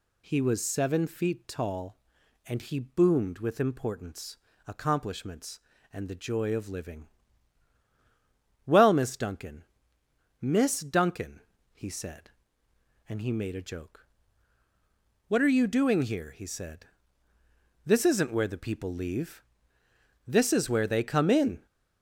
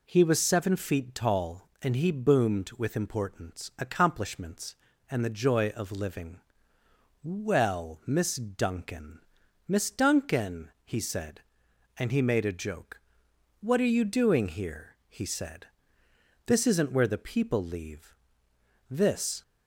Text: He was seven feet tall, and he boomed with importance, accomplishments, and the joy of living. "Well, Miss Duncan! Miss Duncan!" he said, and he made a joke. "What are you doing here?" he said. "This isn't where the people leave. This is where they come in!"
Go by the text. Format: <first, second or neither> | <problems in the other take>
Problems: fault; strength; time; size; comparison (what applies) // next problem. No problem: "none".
first | stops before "is where they come in"; at 19.4 s